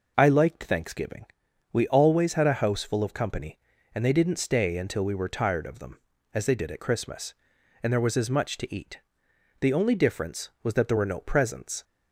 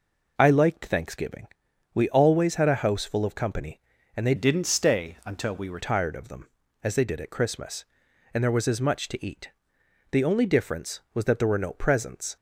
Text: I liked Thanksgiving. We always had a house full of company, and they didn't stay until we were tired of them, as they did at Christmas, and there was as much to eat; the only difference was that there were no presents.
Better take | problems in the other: first | changes voice from "didn't" to "were"; from 4.3 to 5.7 s; 1.4 s long

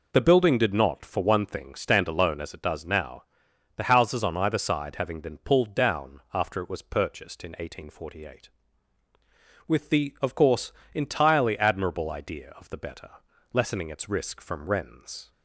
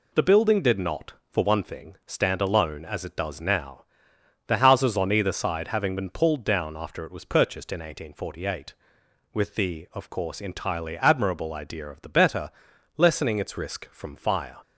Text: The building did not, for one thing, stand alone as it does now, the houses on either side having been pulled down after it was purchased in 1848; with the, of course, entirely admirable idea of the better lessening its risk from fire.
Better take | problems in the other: second | pauses between "better" and "lessening"; at 13.1 s; 0.42 s long; noticeable in the second // says "wrens" for "fire"; at 14.6 s

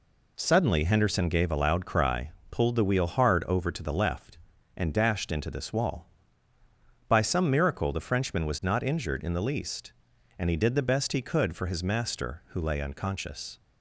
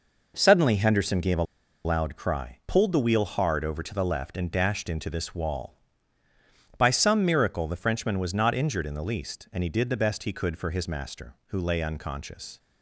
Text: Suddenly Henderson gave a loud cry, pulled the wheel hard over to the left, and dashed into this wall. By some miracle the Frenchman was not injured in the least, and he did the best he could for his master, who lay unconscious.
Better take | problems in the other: first | pauses between "a" and "loud"; at 1.4 s; 0.41 s long

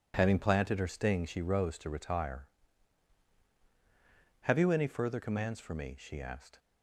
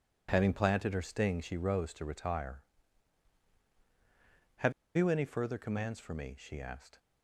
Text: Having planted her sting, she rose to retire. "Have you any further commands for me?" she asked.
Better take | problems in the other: first | pauses between "Have" and "you"; slight; at 4.7 s; 0.25 s long

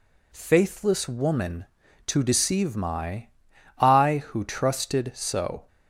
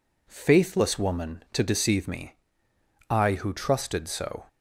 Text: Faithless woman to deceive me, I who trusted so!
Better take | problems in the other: second | says "my" for "me"; at 2.7 s

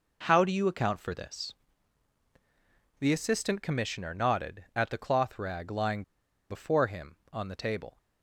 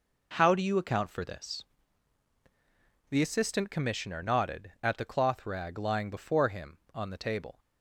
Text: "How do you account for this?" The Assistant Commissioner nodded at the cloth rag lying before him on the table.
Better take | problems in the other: second | pauses between "lying" and "before"; noticeable; at 6.0 s; 0.46 s long

